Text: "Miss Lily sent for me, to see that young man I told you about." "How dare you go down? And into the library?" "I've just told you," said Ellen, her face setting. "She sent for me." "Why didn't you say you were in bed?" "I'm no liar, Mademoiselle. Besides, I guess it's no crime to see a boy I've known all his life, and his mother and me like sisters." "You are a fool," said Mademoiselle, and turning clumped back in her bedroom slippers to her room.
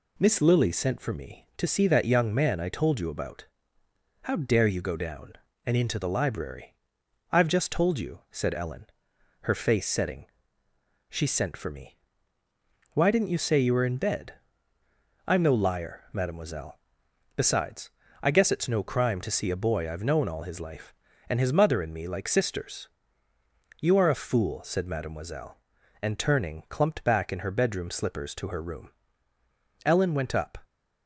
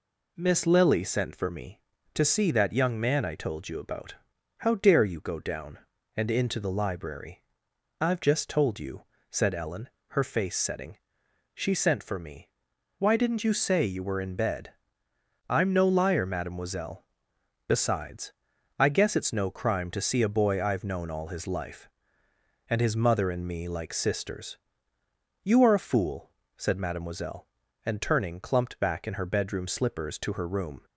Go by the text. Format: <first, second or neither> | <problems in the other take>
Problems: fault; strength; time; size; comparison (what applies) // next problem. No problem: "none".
second | goes on to say "Ellen went up"; noticeable; from 29.8 s on; 0.72 s long